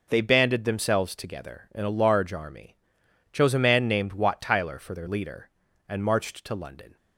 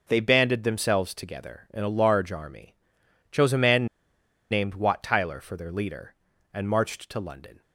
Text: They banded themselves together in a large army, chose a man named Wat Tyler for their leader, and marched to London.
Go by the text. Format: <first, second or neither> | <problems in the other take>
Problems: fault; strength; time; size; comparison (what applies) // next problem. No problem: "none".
first | pauses between "man" and "named"; noticeable; at 3.8 s; 0.65 s long